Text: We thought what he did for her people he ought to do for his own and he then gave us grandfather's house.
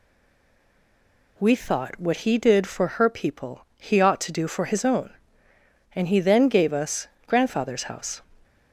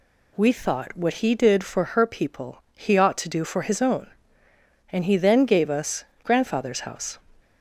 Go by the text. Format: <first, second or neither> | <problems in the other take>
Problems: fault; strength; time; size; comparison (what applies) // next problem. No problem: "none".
second | stays silent before the first word; noticeable; until 1.3 s; 1.3 s long // pauses between "us" and "grandfather's"; slight; at 7.0 s; 0.18 s long; slight in the second